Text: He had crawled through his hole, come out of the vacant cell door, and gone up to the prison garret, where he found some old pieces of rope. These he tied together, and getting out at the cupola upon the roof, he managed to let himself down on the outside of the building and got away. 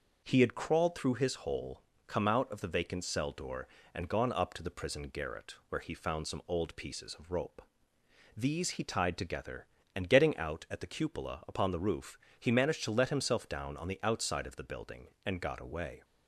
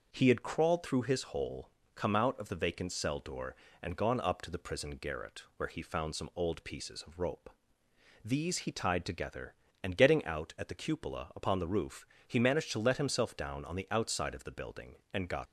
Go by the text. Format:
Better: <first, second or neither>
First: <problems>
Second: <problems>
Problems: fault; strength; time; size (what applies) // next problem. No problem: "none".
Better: first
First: none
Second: stops before "away"; at 15.4 s